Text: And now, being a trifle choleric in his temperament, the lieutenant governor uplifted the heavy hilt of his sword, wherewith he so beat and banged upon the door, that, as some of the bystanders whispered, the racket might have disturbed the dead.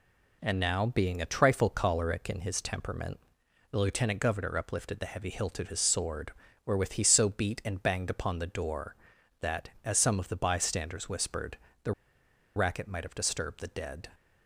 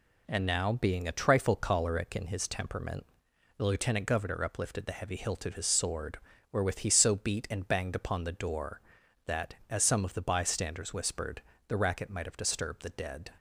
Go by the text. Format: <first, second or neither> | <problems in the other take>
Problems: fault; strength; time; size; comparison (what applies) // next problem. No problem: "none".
second | pauses between "the" and "racket"; noticeable; at 11.9 s; 0.63 s long